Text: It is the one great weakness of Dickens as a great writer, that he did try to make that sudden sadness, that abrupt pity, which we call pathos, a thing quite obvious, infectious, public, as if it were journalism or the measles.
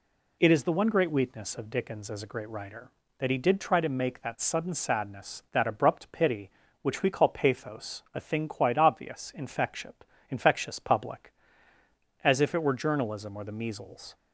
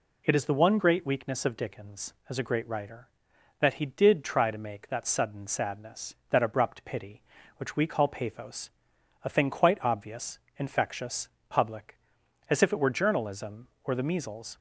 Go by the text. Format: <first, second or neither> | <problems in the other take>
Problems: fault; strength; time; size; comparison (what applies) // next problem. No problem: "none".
second | says "infectious" twice; at 10.3 s